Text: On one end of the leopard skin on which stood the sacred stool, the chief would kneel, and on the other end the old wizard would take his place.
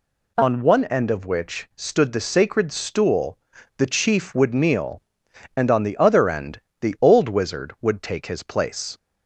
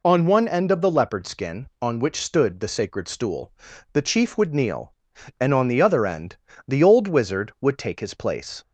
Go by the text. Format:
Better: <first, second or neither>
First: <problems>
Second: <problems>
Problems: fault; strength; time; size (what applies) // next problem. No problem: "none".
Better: second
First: skips "the leopard skin on"; at 1.2 s // pauses between "end" and "the"; slight; at 6.5 s; 0.22 s long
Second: pauses between "end" and "the"; slight; at 6.3 s; 0.32 s long